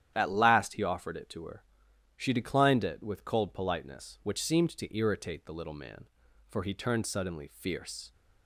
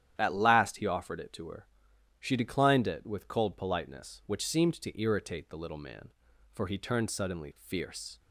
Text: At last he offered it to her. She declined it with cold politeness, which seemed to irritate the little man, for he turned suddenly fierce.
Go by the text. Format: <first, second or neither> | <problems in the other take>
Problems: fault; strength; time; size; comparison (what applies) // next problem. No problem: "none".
neither | starts louder than the rest; strong; the same in both